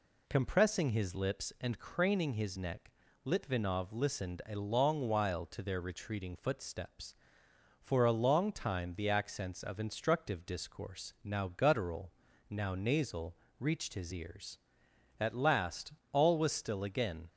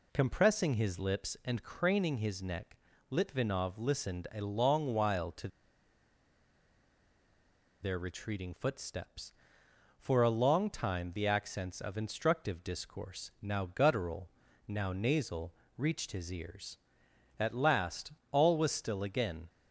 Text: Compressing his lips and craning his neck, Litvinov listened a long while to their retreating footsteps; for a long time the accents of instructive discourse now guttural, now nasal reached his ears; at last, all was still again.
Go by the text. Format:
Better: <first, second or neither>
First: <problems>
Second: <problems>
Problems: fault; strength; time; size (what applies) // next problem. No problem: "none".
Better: first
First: pauses between "nasal" and "reached"; slight; at 13.3 s; 0.24 s long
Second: pauses between "to" and "their"; strong; at 5.4 s; 2.3 s long // pauses between "nasal" and "reached"; slight; at 15.5 s; 0.24 s long